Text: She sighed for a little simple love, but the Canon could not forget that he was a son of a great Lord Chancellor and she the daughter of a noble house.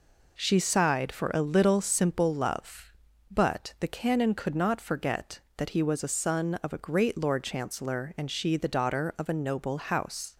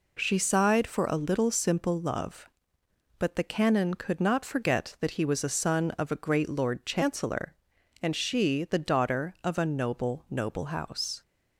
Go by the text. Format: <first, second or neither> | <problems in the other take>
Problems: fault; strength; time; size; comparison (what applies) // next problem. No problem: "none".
first | says "noble" twice; at 10.2 s